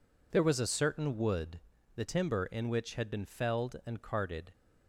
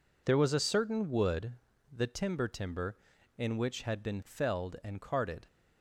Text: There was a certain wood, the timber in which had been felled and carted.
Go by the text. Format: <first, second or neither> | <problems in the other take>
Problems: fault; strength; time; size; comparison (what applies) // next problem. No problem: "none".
first | says "timber" twice; at 2.4 s